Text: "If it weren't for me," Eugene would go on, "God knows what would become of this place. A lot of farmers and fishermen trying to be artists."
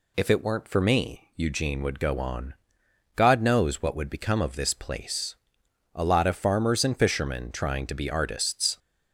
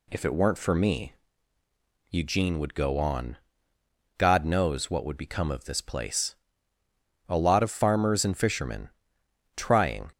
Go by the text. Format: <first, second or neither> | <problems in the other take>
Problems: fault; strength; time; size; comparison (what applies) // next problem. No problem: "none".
first | pauses between "fishermen" and "trying"; noticeable; at 8.8 s; 0.66 s long // stops before "to be artists"; at 10.1 s